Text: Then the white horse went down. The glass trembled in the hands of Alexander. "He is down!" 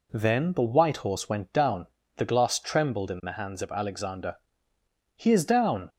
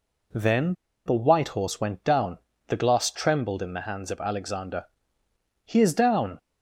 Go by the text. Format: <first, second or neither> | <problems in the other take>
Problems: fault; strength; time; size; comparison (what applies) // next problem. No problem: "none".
first | pauses between "Then" and "the"; slight; at 0.7 s; 0.32 s long